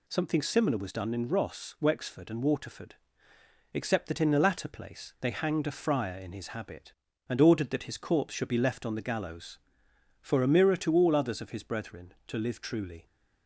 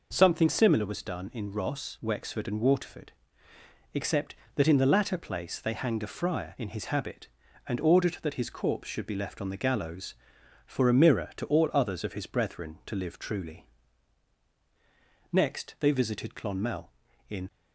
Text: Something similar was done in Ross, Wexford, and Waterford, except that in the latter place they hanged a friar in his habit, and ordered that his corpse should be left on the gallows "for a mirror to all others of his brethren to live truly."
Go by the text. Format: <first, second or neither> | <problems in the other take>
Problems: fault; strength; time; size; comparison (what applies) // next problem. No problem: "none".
first | goes on to say "Next they visited Clonmel in"; strong; from 15.3 s on; 2.1 s long